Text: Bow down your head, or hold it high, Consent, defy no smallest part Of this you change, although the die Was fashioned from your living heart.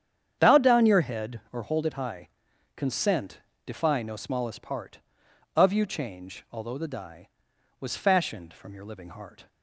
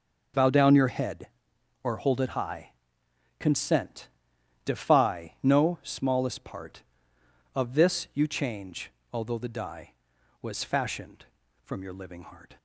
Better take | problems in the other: second | starts louder than the rest; strong; until 1.4 s; 8.5 dB; noticeable in the second // skips "this"; at 5.7 s

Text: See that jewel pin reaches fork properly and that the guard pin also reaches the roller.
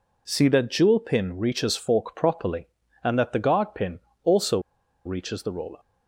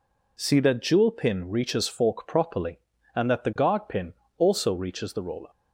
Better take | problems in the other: second | pauses between "pin" and "also"; slight; at 3.9 s; 0.24 s long; slight in the second // pauses between "also" and "reaches"; noticeable; at 4.5 s; 0.46 s long

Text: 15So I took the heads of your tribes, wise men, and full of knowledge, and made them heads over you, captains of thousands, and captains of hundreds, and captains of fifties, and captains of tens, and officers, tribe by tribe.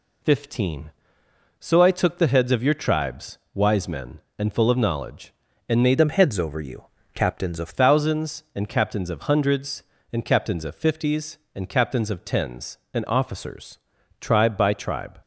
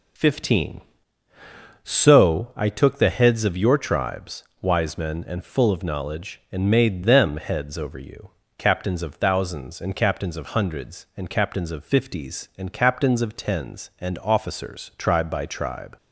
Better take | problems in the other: second | changes voice from "them" to "of"; from 5.9 to 7.6 s; 1.7 s long

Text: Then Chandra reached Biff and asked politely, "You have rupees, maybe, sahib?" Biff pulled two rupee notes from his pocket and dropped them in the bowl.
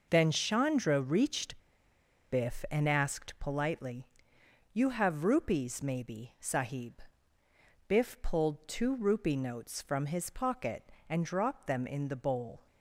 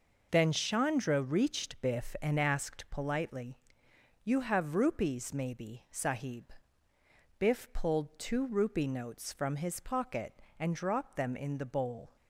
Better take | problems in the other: second | pauses between "reached" and "Biff"; noticeable; at 1.5 s; 0.72 s long

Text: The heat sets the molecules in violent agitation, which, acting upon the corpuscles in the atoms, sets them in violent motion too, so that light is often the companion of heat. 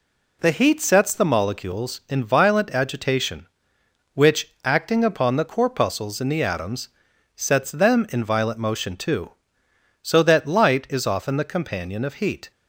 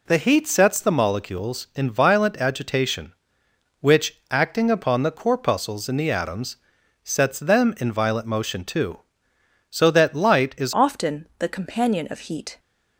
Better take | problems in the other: first | changes voice at "often"; from 10.7 s on; 1.8 s long

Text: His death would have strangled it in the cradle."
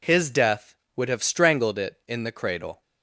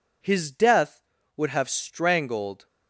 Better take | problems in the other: first | stops before "it in the cradle"; at 2.6 s

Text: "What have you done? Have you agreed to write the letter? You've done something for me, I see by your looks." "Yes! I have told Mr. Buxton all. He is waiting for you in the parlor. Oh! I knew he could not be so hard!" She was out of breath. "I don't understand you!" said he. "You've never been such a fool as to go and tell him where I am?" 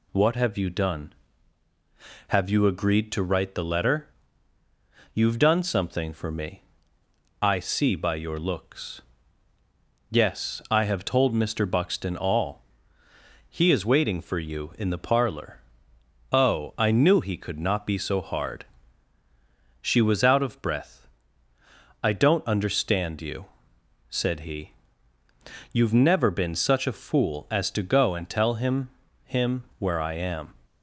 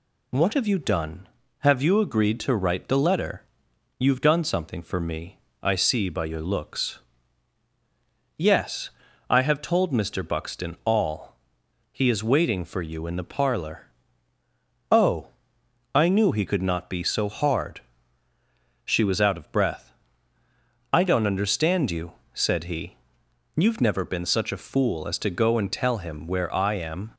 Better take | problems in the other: second | says "him" twice; at 29.2 s

